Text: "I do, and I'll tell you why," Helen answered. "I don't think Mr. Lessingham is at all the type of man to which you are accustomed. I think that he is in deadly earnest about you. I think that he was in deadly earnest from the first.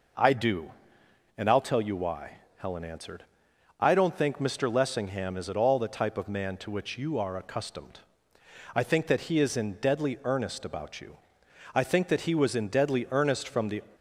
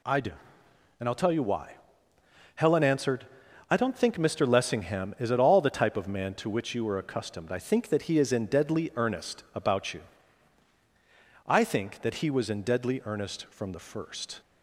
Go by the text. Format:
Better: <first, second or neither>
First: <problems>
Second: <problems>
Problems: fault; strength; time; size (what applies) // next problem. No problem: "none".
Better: second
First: stops before "first"; at 13.9 s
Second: none